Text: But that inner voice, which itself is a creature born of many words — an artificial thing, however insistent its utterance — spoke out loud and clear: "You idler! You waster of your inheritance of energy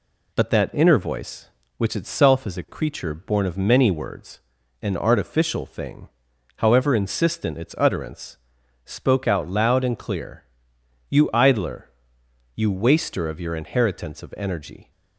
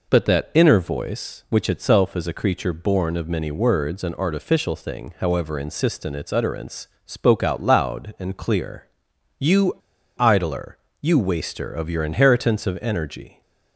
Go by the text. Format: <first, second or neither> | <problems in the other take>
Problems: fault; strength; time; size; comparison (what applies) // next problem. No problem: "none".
first | pauses between "You" and "idler"; at 9.7 s; 0.42 s long